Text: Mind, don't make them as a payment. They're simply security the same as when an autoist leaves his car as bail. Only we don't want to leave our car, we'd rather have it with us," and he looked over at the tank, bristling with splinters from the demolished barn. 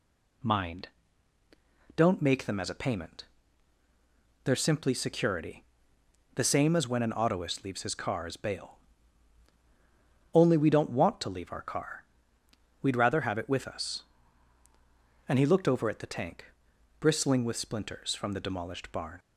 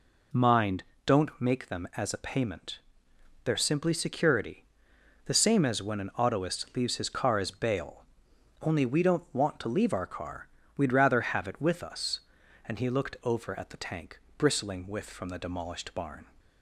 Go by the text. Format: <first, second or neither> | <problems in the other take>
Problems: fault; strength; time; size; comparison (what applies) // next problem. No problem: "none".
first | pauses between "security" and "the"; noticeable; at 4.6 s; 0.60 s long; noticeable in the first // skips "splinters"; at 15.0 s